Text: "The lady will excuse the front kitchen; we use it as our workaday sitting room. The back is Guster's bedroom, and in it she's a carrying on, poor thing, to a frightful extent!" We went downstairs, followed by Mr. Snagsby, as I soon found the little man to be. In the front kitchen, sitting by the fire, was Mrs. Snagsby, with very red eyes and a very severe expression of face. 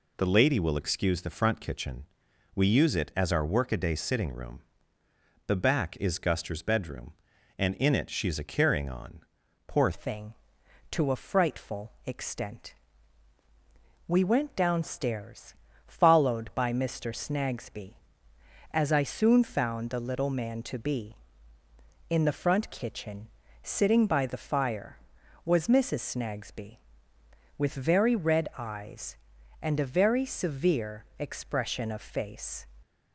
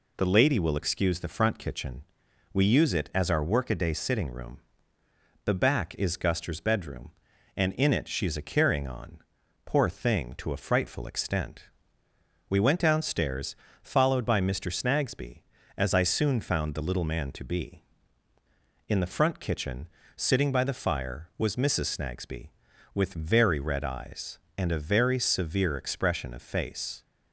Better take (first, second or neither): second